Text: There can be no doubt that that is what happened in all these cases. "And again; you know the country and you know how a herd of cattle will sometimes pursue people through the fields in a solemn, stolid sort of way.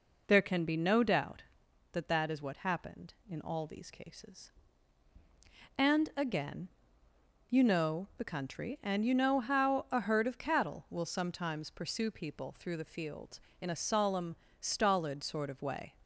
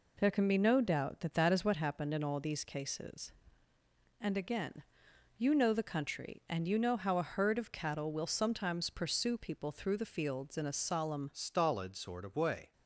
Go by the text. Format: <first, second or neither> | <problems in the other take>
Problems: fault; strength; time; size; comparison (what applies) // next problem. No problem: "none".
first | changes voice at "stolid"; from 11.3 s on; 1.4 s long